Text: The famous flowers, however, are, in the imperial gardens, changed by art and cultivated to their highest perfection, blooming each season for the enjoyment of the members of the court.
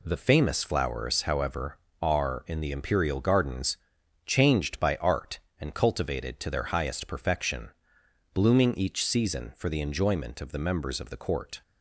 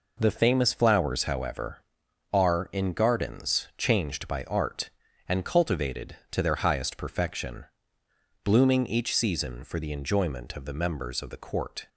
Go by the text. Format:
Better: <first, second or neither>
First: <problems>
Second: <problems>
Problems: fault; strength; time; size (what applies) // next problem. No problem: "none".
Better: first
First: none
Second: skips "the imperial"; at 2.9 s